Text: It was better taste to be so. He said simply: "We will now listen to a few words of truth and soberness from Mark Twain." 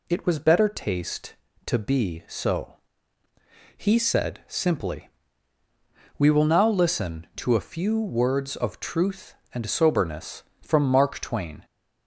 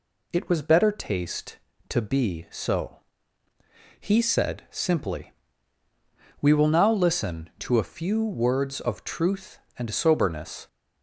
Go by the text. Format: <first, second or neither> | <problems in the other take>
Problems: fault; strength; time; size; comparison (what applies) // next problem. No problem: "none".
first | stops before "from Mark Twain"; at 10.6 s